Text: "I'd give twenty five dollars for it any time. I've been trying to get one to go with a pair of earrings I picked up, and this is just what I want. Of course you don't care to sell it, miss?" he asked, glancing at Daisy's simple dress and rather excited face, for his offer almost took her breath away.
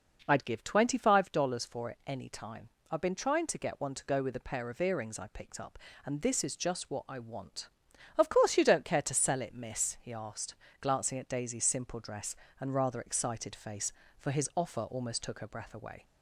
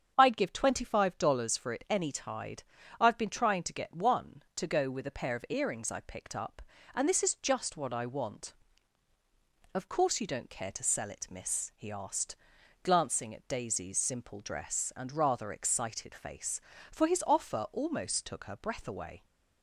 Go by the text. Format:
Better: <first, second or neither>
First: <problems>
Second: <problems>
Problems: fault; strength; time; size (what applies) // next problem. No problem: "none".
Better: first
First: none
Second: starts louder than the rest; strong; until 1.1 s; 7.5 dB // says "tide" for "time"; at 2.1 s